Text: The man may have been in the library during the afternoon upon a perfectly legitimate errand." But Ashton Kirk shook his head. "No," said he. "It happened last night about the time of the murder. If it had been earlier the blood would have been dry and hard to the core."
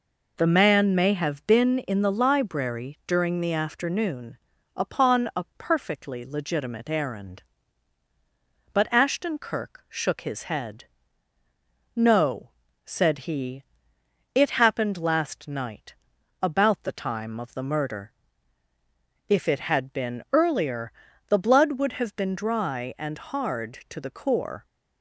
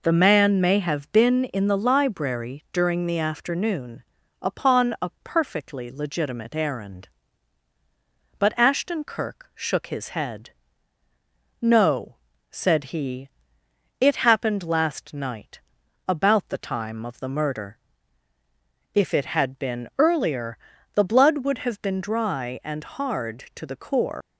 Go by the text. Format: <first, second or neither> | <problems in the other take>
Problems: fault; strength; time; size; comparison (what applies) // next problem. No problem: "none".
first | pauses between "afternoon" and "upon"; at 4.0 s; 0.38 s long; also in the first // pauses between "night" and "about"; noticeable; at 15.6 s; 0.48 s long; noticeable in the first // pauses between "earlier" and "the"; at 20.5 s; 0.38 s long; also in the first // leaves "core" unfinished; at 24.2 s; 100 ms